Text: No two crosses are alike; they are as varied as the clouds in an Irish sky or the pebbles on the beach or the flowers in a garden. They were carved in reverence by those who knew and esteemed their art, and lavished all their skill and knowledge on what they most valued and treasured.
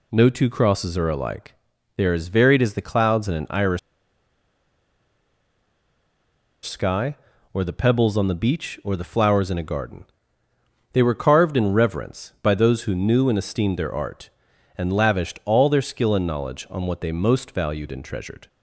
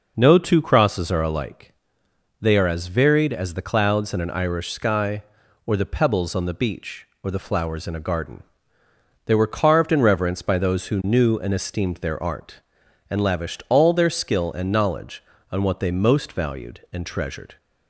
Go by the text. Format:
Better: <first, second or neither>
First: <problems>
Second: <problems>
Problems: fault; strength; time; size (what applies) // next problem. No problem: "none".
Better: second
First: pauses between "Irish" and "sky"; strong; at 3.7 s; 2.8 s long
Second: none